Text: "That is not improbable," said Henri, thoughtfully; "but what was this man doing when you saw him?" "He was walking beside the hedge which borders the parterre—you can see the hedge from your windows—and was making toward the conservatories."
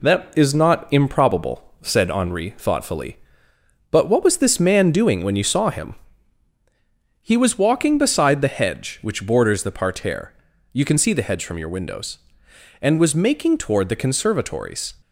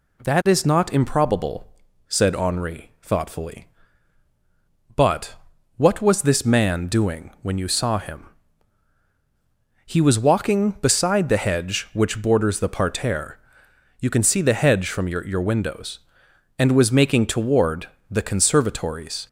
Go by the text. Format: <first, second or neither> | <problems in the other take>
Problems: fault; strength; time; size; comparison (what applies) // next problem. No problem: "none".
first | pauses between "but" and "what"; at 5.3 s; 0.44 s long // says "your" twice; at 15.2 s // pauses between "toward" and "the"; slight; at 17.8 s; 0.20 s long